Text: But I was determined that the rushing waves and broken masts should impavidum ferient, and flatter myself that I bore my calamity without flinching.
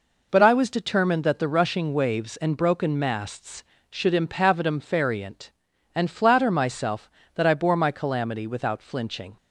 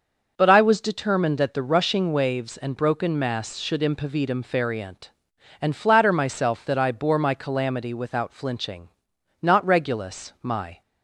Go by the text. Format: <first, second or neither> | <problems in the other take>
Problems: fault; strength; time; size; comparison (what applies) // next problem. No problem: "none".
first | starts louder than the rest; noticeable; until 1.3 s; 6 dB // goes on to say "Not Regulus my"; from 9.4 s on; 1.4 s long